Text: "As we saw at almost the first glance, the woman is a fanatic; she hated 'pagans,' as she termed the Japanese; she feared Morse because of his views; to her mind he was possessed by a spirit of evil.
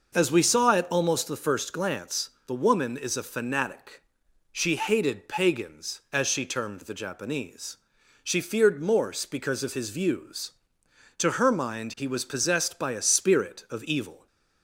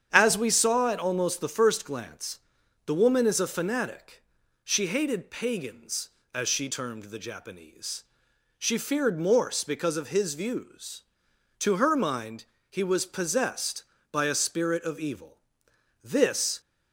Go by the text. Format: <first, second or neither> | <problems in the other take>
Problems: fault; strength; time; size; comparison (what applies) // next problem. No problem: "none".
first | starts louder than the rest; strong; until 1.1 s; 8.5 dB; noticeable in the first // pauses between "mind" and "he"; slight; at 12.4 s; 0.26 s long // goes on to say "This"; from 16.0 s on; 0.56 s long